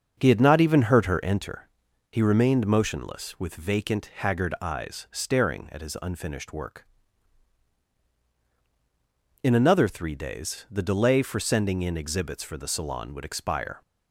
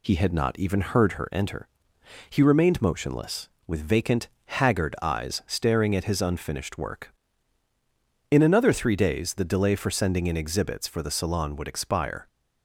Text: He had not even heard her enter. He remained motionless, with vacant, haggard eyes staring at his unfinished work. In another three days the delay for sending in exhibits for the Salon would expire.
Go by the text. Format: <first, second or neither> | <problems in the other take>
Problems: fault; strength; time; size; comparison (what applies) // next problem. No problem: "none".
second | starts louder than the rest; until 1.2 s; 6.5 dB